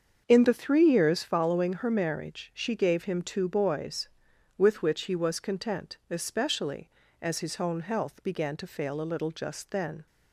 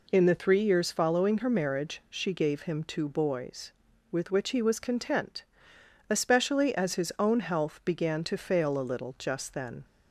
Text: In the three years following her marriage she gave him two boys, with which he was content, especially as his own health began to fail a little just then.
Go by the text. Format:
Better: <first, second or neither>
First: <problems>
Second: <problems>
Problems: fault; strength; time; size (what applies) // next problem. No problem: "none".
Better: second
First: starts louder than the rest; until 1.3 s; 7 dB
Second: none